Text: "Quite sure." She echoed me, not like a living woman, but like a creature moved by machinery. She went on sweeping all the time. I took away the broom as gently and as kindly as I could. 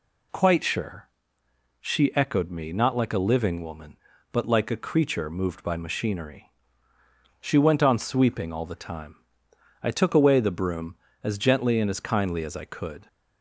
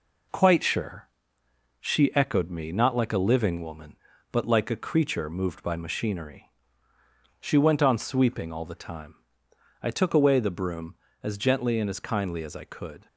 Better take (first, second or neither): first